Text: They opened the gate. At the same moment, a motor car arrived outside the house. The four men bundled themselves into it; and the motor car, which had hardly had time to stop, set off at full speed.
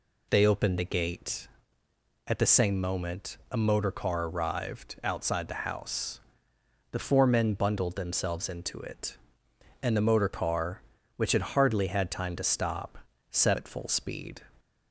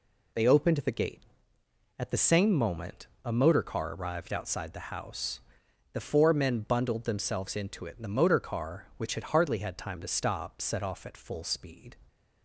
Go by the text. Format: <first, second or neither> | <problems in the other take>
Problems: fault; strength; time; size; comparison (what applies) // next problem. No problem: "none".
second | skips "off"; at 13.5 s